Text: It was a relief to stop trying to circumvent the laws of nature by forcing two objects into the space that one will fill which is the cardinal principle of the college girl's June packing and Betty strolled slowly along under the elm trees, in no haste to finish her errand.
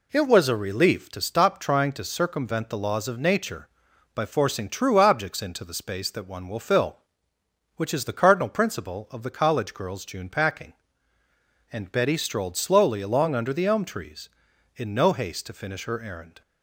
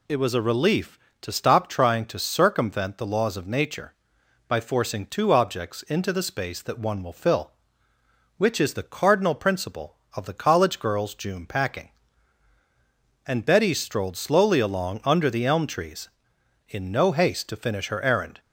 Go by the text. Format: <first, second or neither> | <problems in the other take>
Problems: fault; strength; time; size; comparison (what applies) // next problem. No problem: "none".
second | says "true" for "two"; at 4.6 s